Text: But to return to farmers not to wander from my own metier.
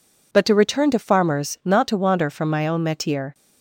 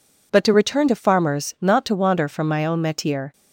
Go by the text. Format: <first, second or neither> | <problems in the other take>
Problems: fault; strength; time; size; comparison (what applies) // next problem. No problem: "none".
neither | none